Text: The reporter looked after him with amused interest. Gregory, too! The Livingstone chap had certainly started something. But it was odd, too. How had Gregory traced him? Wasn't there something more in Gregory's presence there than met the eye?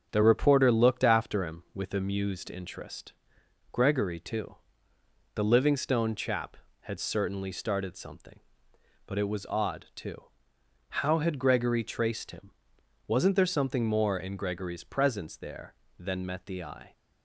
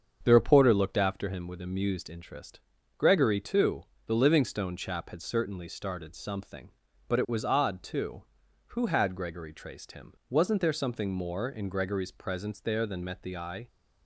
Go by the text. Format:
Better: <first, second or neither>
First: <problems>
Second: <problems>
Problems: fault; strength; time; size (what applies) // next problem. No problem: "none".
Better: first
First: starts louder than the rest; strong; until 1.1 s; 7 dB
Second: starts louder than the rest; strong; until 1.2 s; 7 dB // says "Who" for "How"; at 8.6 s